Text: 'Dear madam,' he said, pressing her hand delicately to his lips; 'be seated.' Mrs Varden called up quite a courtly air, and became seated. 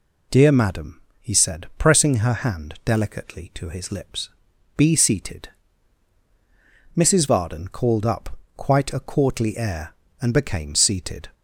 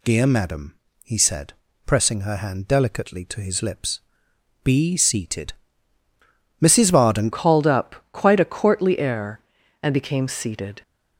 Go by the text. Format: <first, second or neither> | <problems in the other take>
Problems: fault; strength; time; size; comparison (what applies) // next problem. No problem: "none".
first | changes voice at "called"; from 7.3 s on; 3.5 s long // pauses between "up" and "quite"; slight; at 7.9 s; 0.16 s long; slight in the first